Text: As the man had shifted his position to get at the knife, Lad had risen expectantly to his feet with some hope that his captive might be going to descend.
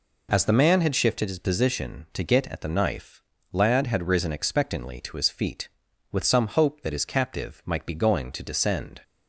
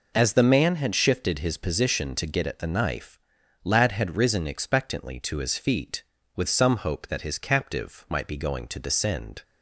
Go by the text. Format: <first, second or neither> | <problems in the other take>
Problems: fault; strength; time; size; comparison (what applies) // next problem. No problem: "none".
neither | none